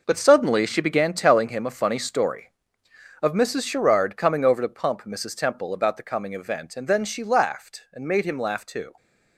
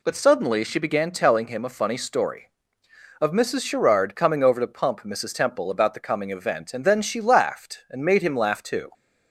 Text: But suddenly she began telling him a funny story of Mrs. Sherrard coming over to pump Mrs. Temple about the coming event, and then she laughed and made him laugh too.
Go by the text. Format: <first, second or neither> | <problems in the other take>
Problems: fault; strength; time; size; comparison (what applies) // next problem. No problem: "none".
second | gets quieter; strong; throughout; 10.5 dB